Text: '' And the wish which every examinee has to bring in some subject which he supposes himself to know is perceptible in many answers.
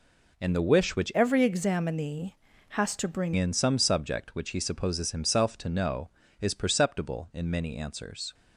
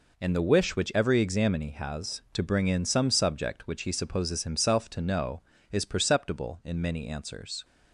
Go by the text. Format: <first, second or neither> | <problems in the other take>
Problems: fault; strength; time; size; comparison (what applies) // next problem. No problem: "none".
second | changes voice from "every" to "bring"; from 1.1 to 3.3 s; 2.2 s long